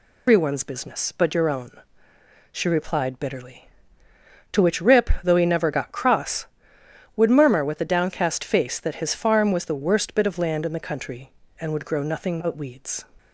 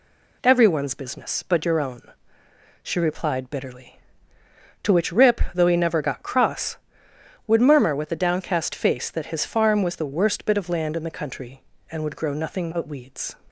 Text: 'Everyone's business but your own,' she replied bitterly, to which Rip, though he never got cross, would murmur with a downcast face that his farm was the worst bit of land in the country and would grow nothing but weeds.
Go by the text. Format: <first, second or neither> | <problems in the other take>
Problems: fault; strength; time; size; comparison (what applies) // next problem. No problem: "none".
second | loses the start of "Everyone's"; at 0.2 s; 170 ms